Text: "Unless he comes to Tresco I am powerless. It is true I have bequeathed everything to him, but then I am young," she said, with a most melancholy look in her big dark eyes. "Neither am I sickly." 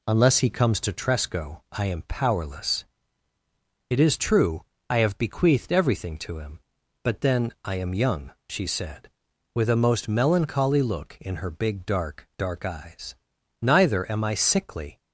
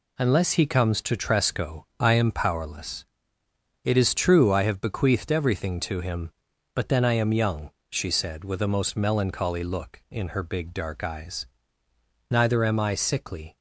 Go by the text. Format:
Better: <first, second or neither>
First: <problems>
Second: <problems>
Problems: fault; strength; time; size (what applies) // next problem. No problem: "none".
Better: second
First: pauses between "true" and "I"; slight; at 4.6 s; 0.24 s long // says "dark" twice; at 12.3 s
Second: none